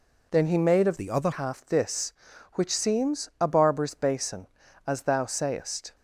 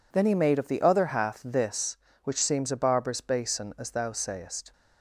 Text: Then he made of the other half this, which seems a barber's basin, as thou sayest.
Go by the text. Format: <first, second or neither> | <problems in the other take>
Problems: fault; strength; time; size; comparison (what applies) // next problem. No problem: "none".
second | changes voice from "the" to "other"; from 0.9 to 1.3 s; 0.4 s long